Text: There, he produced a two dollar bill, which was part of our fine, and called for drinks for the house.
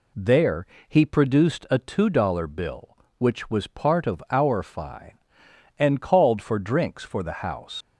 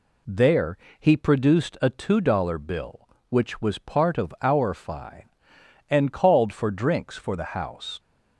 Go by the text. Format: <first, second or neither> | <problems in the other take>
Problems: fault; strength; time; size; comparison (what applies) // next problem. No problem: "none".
second | leaves "house" unfinished; at 7.8 s; 65 ms